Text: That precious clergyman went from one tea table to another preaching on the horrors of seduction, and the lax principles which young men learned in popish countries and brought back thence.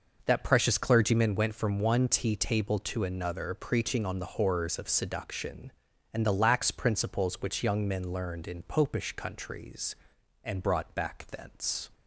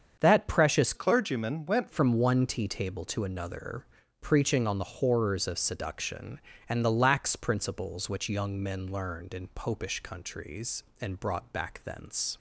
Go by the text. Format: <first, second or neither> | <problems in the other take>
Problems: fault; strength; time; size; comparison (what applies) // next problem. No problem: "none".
first | starts louder than the rest; strong; until 1.2 s; 7.5 dB // changes voice from "clergyman" to "went"; from 0.9 to 1.8 s; 0.9 s long // pauses between "another" and "preaching"; slight; at 3.8 s; 0.34 s long